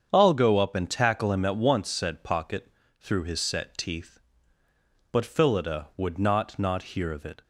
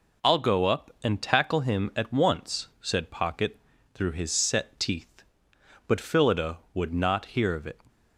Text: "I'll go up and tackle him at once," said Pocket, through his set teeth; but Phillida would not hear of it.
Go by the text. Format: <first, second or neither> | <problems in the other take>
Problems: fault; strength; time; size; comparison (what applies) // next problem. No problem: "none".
second | starts louder than the rest; strong; until 1.1 s; 7.5 dB // says "not" twice; at 6.5 s